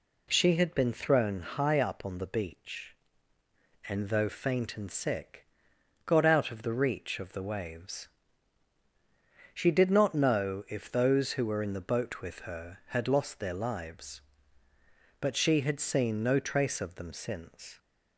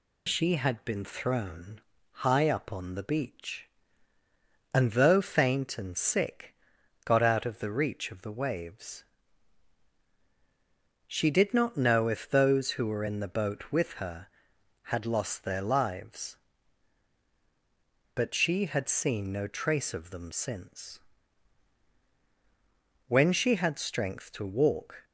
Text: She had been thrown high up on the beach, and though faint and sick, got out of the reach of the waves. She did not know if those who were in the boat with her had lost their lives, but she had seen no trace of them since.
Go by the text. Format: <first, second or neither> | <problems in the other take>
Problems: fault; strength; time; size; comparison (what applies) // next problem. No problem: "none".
first | pauses between "thrown" and "high"; slight; at 1.7 s; 0.32 s long // goes on to say "When she had strength to walk"; strong; from 23.0 s on; 1.9 s long